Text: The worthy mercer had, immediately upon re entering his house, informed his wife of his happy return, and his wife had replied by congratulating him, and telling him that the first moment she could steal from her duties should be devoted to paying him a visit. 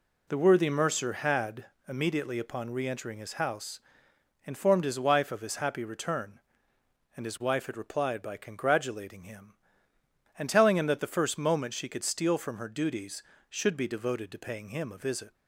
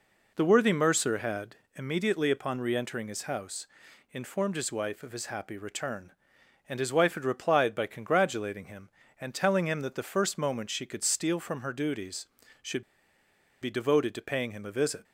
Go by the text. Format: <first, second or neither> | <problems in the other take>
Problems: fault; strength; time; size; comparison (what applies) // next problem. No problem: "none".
first | pauses between "should" and "be"; noticeable; at 12.8 s; 0.80 s long